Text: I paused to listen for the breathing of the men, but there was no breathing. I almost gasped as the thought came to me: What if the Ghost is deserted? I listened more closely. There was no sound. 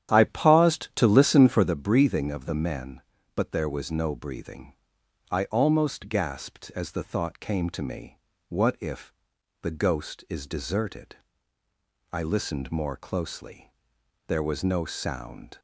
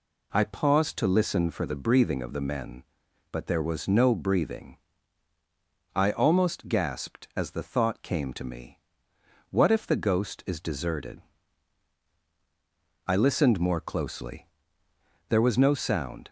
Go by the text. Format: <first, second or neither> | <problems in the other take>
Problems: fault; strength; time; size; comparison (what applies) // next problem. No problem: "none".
second | starts louder than the rest; strong; until 1.7 s; 10 dB // pauses between "if" and "the"; noticeable; at 9.1 s; 0.48 s long